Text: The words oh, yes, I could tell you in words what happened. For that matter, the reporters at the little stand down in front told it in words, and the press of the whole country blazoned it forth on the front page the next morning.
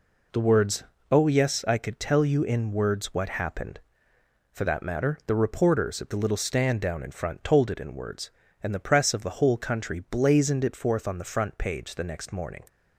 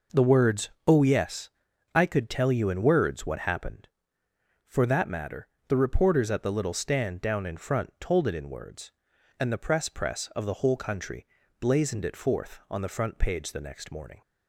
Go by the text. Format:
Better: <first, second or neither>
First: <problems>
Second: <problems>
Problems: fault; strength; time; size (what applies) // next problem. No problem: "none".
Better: first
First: pauses between "words" and "oh"; slight; at 0.8 s; 0.28 s long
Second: pauses between "words" and "oh"; slight; at 0.7 s; 0.18 s long // says "press" twice; at 9.8 s // pauses between "country" and "blazoned"; slight; at 11.2 s; 0.32 s long